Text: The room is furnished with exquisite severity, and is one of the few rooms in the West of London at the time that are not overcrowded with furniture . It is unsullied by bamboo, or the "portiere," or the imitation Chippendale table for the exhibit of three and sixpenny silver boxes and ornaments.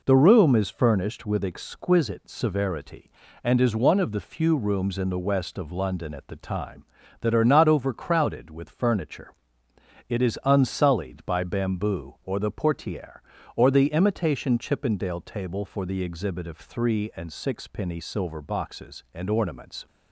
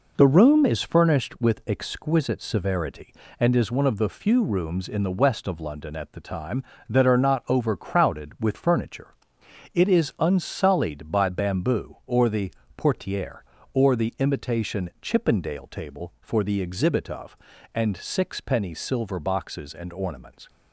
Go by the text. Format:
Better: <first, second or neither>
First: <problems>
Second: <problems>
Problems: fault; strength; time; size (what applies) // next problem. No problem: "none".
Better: first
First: none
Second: pauses between "the" and "portiere"; slight; at 12.5 s; 0.28 s long // skips "three"; at 17.5 s